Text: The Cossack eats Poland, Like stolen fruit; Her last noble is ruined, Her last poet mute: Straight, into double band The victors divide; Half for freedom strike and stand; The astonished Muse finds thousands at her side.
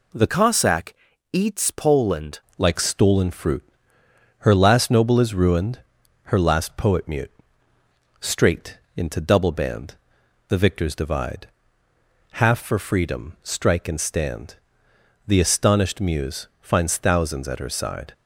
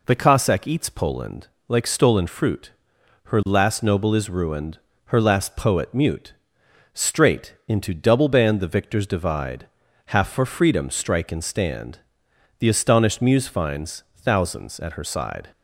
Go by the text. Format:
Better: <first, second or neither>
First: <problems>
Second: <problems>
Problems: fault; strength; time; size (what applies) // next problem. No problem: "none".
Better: second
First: changes voice from "Cossack" to "Poland"; from 0.2 to 2.3 s; 2.1 s long // pauses between "Cossack" and "eats"; at 0.9 s; 0.38 s long // pauses between "band" and "The"; noticeable; at 9.9 s; 0.54 s long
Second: none